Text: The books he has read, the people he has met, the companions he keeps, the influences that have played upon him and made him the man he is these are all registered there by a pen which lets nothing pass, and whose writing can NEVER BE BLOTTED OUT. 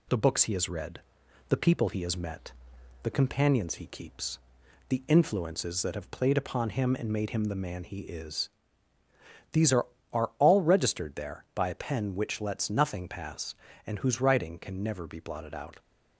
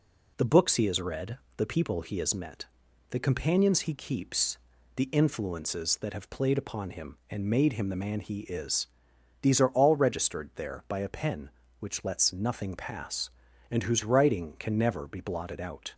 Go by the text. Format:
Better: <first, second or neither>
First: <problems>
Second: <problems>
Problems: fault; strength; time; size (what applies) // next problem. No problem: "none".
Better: second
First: pauses between "is" and "these"; at 8.4 s; 1.0 s long // says "are" twice; at 10.1 s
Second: pauses between "is" and "these"; noticeable; at 8.8 s; 0.54 s long